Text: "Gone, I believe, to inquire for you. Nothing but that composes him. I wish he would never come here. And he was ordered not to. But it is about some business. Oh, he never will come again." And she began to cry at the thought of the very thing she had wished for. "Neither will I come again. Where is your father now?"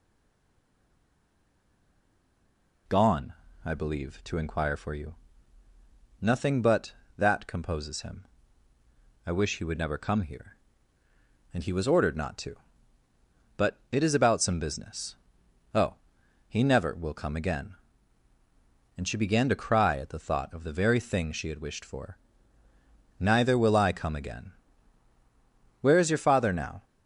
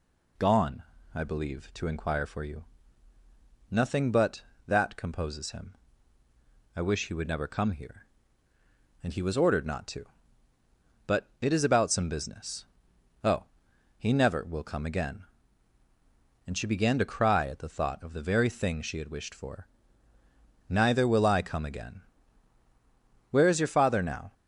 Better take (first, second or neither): second